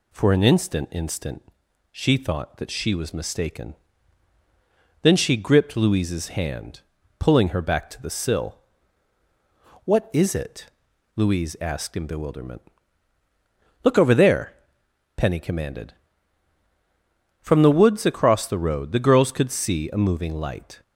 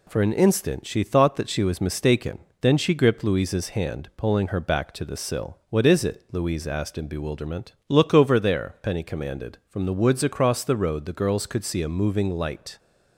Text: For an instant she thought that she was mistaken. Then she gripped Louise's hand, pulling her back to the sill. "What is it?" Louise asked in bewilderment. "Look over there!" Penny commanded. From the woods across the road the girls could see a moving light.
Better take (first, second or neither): second